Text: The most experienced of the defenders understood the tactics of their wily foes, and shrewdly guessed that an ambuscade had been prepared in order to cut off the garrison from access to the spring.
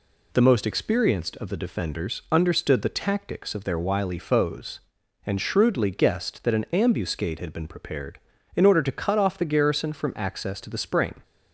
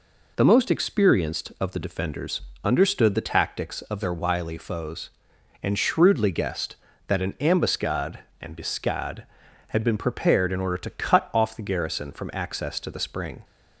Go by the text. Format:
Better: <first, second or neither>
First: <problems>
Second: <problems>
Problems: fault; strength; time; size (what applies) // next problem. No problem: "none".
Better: first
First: none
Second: pauses between "defenders" and "understood"; slight; at 2.4 s; 0.22 s long // says "ambuscade" twice; at 8.4 s